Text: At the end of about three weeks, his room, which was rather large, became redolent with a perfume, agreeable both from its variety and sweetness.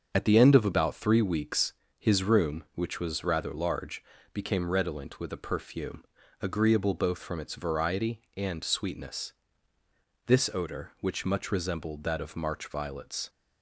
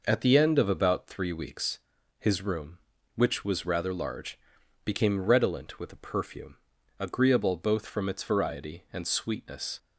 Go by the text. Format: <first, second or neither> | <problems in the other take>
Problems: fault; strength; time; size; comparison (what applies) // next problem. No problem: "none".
second | starts louder than the rest; until 1.1 s; 7 dB // goes on to say "This odor which much resembled that of March violets"; strong; from 10.2 s on; 3.0 s long